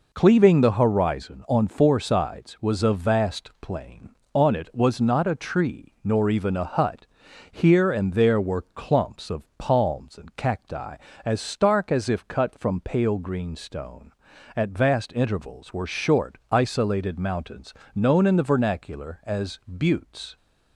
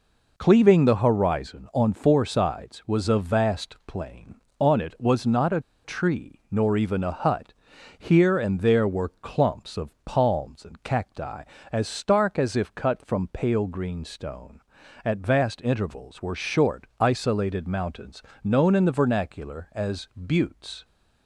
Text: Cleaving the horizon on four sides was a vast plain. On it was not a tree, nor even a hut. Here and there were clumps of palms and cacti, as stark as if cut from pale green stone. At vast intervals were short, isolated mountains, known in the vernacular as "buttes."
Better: first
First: pauses between "of" and "palms"; slight; at 9.4 s; 0.16 s long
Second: pauses between "a" and "tree"; slight; at 5.6 s; 0.23 s long // pauses between "of" and "palms"; slight; at 9.8 s; 0.16 s long

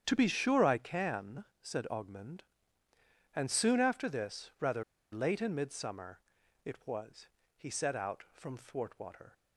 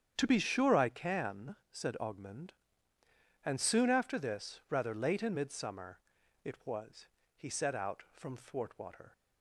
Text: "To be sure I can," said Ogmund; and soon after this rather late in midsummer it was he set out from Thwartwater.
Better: second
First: starts louder than the rest; strong; until 1.0 s; 8.5 dB // pauses between "rather" and "late"; slight; at 4.8 s; 0.29 s long // pauses between "midsummer" and "it"; noticeable; at 6.1 s; 0.46 s long // pauses between "was" and "he"; slight; at 7.2 s; 0.28 s long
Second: starts louder than the rest; strong; until 1.1 s; 8.5 dB // pauses between "midsummer" and "it"; noticeable; at 5.9 s; 0.46 s long // pauses between "was" and "he"; slight; at 7.0 s; 0.28 s long

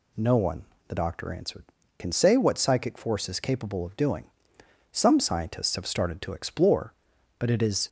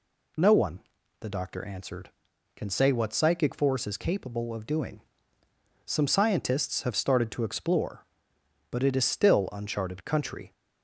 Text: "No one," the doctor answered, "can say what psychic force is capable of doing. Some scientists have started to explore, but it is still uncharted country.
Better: second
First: stops before "still uncharted country"; at 7.8 s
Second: none

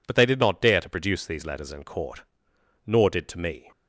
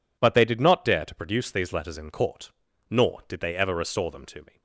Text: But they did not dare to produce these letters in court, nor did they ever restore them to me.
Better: second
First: skips "they ever restore them"; at 3.2 s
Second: none

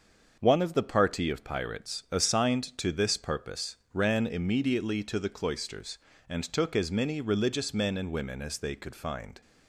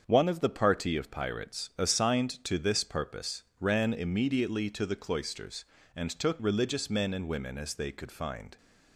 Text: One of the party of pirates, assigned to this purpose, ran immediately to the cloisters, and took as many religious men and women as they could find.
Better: first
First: starts louder than the rest; until 1.4 s; 6.5 dB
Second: starts louder than the rest; until 1.0 s; 7 dB // skips "as many"; at 6.3 s

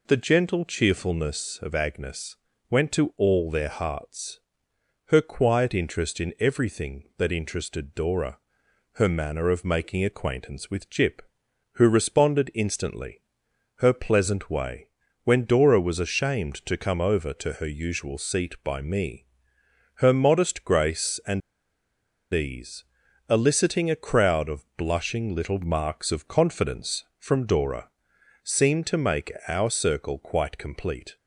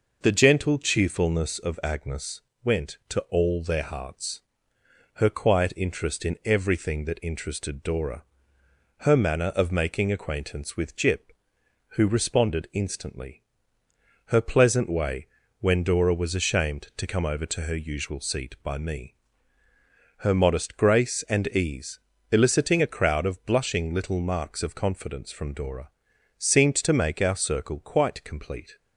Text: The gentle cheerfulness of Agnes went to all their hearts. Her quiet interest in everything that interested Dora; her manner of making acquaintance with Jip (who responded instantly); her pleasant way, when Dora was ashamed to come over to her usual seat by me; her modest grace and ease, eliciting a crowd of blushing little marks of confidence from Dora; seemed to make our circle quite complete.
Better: second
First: pauses between "Agnes" and "went"; slight; at 2.3 s; 0.34 s long // pauses between "and" and "ease"; noticeable; at 21.4 s; 0.91 s long // pauses between "make" and "our"; slight; at 29.3 s; 0.16 s long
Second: pauses between "Agnes" and "went"; slight; at 2.4 s; 0.22 s long

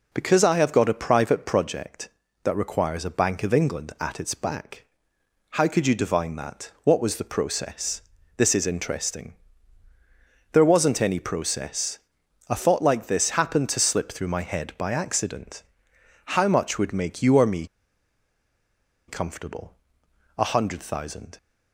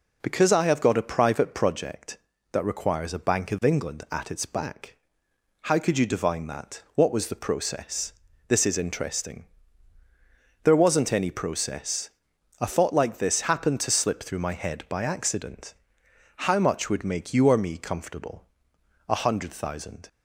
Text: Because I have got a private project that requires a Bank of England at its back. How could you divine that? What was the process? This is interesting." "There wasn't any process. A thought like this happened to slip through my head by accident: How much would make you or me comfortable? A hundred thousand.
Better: second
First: pauses between "me" and "comfortable"; strong; at 17.6 s; 1.4 s long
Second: none

